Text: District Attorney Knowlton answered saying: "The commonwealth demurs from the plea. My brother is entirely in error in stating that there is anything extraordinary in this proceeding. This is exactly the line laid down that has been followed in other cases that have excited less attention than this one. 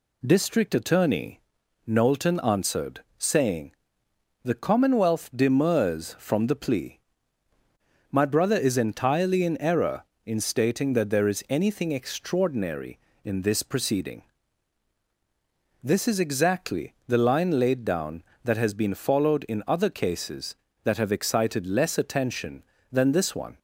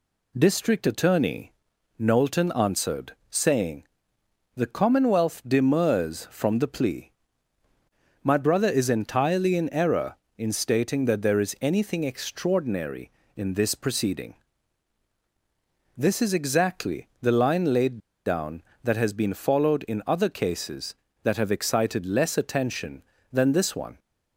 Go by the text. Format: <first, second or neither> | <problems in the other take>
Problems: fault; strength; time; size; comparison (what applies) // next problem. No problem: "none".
first | pauses between "Attorney" and "Knowlton"; noticeable; at 1.5 s; 0.46 s long; noticeable in the first // pauses between "answered" and "saying"; slight; at 3.1 s; 0.16 s long; slight in the first // pauses between "laid" and "down"; slight; at 17.9 s; 0.26 s long